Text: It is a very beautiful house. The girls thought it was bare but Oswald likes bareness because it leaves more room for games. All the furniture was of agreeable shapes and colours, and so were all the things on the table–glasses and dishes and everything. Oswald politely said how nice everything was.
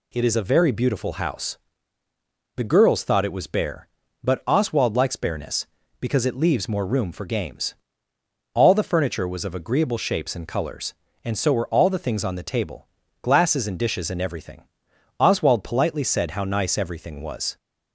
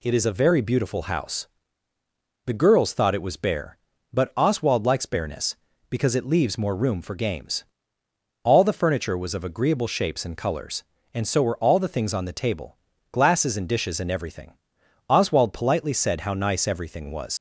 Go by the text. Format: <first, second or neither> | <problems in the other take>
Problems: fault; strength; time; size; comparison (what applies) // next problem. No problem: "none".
first | leaves "was" unfinished; at 17.3 s; 90 ms